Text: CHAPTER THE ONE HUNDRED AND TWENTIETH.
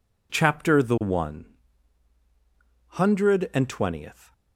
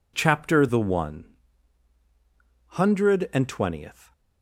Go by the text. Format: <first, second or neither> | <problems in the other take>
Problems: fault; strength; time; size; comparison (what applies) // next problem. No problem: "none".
neither | pauses between "ONE" and "HUNDRED"; strong; the same in both